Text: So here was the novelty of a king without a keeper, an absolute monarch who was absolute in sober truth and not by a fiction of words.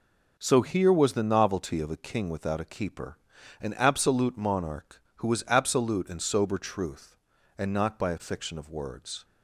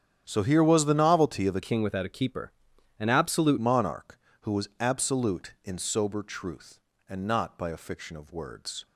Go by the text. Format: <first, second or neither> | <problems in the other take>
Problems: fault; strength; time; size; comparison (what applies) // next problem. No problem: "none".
first | starts louder than the rest; strong; until 1.2 s; 9.5 dB // changes voice from "king" to "absolute"; from 1.6 to 3.5 s; 1.9 s long